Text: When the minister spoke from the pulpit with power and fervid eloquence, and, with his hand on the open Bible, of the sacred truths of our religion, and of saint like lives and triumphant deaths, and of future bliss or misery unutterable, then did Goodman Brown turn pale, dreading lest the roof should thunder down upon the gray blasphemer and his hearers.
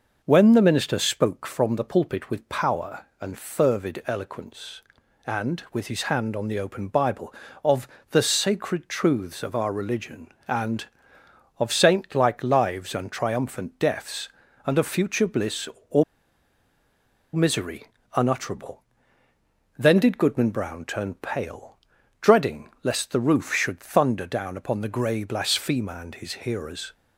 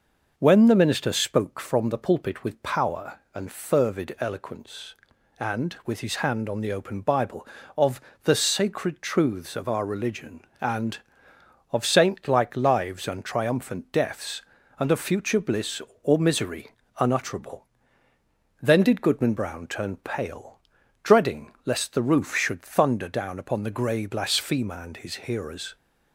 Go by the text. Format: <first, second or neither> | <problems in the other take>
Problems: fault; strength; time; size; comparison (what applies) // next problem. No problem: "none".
second | pauses between "of" and "the"; slight; at 7.8 s; 0.24 s long; slight in the second // pauses between "or" and "misery"; strong; at 16.0 s; 1.2 s long // pauses between "misery" and "unutterable"; slight; at 17.8 s; 0.32 s long; slight in the second